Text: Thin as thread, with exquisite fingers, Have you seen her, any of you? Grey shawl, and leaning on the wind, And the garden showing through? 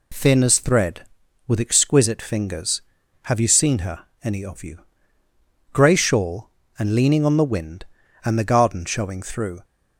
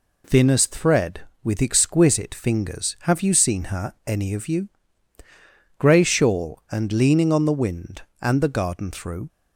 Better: first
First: none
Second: skips "showing"; at 8.9 s

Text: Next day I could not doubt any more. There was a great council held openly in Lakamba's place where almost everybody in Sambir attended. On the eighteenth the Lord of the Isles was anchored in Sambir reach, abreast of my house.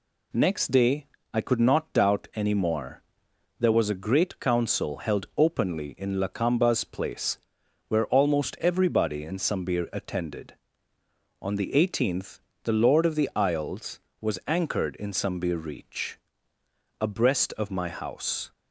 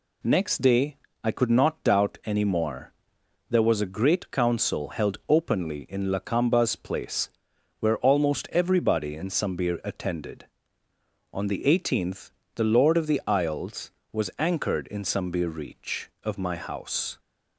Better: first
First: pauses between "day" and "I"; slight; at 1.0 s; 0.26 s long // pauses between "place" and "where"; noticeable; at 7.3 s; 0.50 s long // pauses between "eighteenth" and "the"; slight; at 12.3 s; 0.24 s long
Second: pauses between "day" and "I"; slight; at 0.9 s; 0.26 s long // pauses between "place" and "where"; noticeable; at 7.2 s; 0.50 s long // pauses between "eighteenth" and "the"; slight; at 12.2 s; 0.24 s long // skips "abreast"; at 16.1 s

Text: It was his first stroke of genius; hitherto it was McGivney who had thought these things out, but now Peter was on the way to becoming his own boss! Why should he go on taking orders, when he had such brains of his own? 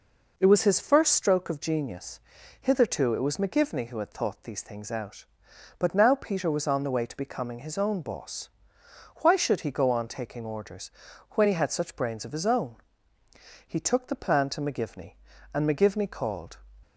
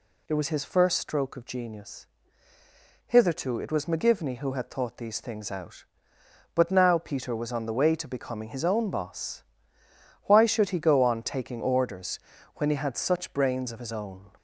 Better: second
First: goes on to say "He took the plan to McGivney and McGivney called"; strong; from 13.6 s on; 2.9 s long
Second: none

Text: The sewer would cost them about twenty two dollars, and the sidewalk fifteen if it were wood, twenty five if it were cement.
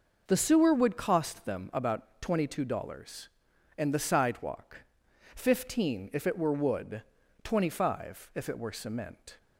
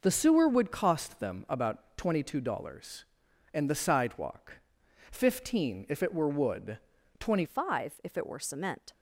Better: first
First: pauses between "sidewalk" and "fifteen"; noticeable; at 4.7 s; 0.58 s long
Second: pauses between "sidewalk" and "fifteen"; noticeable; at 4.5 s; 0.58 s long // changes voice at "five"; from 7.4 s on; 1.5 s long

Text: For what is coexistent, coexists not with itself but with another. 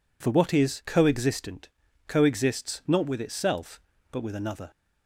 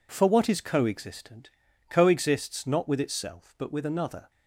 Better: neither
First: none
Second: none

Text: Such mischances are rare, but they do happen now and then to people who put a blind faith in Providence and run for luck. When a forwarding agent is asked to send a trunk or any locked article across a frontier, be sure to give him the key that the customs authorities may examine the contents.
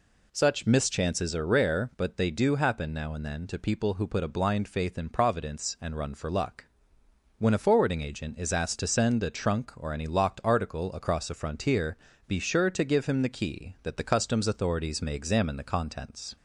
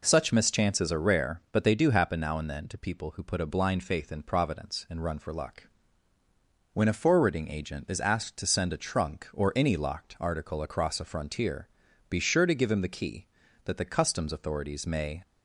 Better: first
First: none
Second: stops before "examine the contents"; at 15.2 s

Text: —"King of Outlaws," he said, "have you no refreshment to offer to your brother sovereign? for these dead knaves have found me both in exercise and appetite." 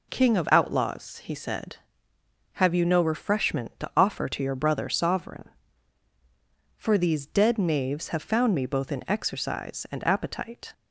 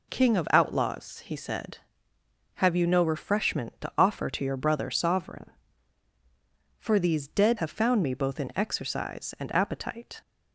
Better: first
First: none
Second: skips "knaves"; at 7.5 s

